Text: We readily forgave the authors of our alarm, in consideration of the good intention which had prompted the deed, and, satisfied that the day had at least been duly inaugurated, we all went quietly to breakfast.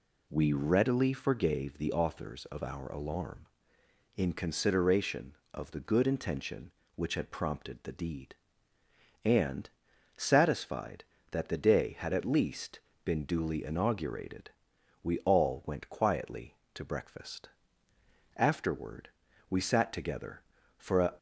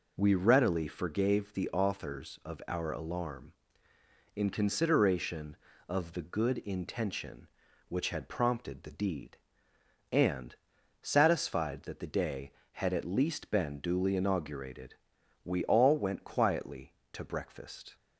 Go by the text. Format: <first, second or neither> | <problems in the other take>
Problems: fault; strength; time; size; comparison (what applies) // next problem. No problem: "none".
second | pauses between "least" and "been"; slight; at 12.7 s; 0.24 s long // goes on to say "Afterward we sat together for a"; strong; from 18.3 s on; 2.7 s long